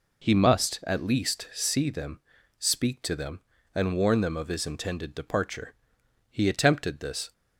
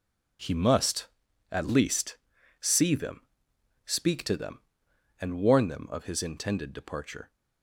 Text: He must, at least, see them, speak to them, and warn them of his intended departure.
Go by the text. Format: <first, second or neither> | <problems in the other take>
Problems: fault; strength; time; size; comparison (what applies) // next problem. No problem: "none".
second | goes on to say "He attempted this"; noticeable; from 6.3 s on; 1.0 s long